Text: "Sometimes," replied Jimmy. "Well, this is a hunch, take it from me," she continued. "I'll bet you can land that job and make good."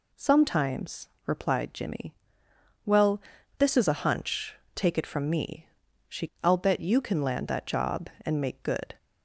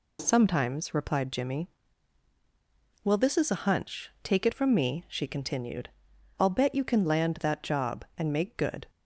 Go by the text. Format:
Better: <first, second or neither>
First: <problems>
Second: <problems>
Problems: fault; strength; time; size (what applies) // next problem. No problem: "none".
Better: second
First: skips "continued"; at 6.3 s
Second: none